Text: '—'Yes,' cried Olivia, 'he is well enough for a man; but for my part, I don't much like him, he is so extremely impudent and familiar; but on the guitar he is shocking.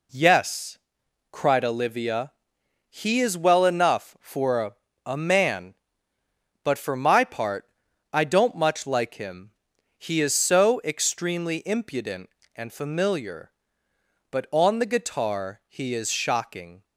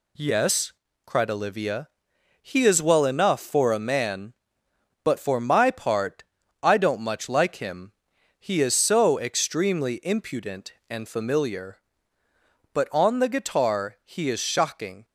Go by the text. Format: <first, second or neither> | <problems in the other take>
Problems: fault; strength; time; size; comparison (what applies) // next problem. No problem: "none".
second | says "a" twice; at 5.0 s